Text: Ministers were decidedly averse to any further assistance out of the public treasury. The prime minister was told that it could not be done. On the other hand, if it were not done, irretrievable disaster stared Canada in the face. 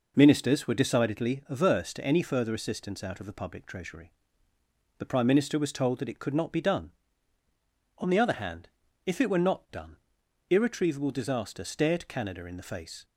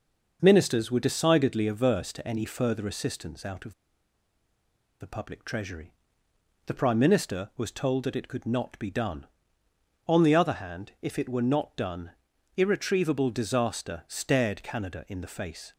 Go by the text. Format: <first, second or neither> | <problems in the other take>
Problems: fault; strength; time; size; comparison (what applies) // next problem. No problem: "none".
first | pauses between "of" and "the"; strong; at 3.7 s; 1.2 s long